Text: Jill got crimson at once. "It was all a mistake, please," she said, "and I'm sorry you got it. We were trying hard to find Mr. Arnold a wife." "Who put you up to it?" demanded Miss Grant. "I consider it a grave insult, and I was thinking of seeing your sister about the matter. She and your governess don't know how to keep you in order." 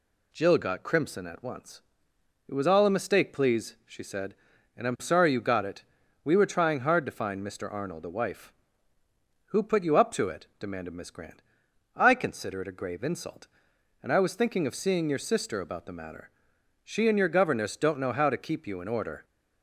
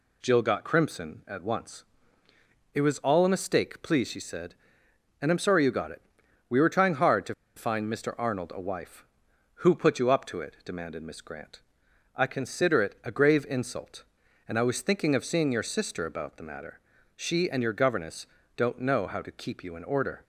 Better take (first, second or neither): first